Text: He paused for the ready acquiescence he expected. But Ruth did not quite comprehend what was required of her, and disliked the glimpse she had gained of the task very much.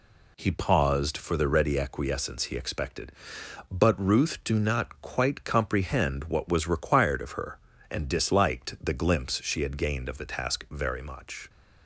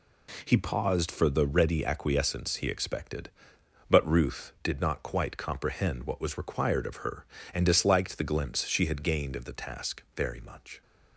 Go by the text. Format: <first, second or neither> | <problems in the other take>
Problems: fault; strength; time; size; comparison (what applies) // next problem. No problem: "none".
second | says "do" for "did"; at 4.4 s